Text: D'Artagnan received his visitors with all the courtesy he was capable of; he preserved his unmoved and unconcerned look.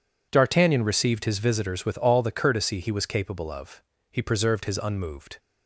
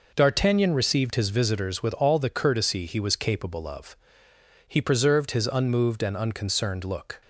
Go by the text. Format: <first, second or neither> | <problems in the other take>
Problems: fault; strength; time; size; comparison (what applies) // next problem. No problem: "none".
second | stops before "and unconcerned look"; at 5.3 s